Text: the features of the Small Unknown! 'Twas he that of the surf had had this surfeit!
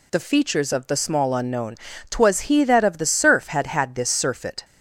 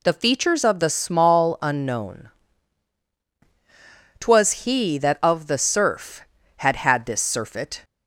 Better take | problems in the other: neither | none

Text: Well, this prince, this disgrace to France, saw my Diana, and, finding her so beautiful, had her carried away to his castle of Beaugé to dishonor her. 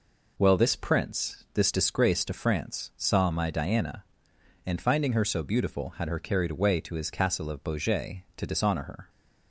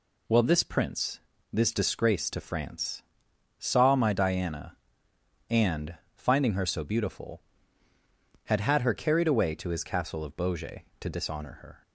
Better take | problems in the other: first | says "had" twice; at 8.5 s

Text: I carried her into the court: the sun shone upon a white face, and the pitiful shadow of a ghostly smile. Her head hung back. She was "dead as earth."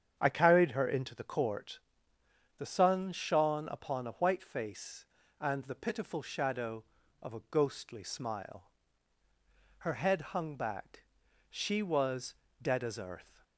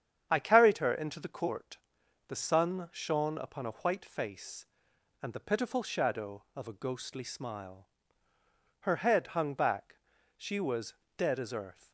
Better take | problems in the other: neither | starts louder than the rest; strong; the same in both // pauses between "was" and "dead"; slight; the same in both

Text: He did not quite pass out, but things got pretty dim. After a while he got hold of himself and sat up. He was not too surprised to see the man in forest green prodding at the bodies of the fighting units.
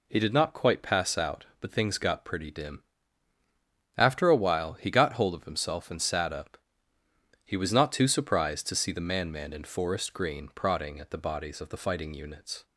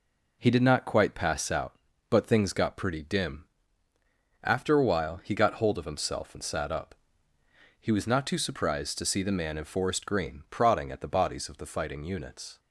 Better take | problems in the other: second | says "man" twice; at 9.3 s

